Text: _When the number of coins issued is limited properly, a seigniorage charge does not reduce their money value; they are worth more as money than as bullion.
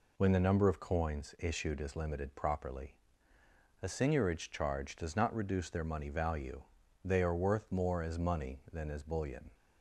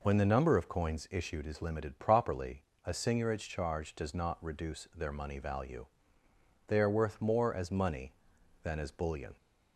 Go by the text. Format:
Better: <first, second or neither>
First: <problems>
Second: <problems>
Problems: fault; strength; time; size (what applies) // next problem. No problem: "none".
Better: neither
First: none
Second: none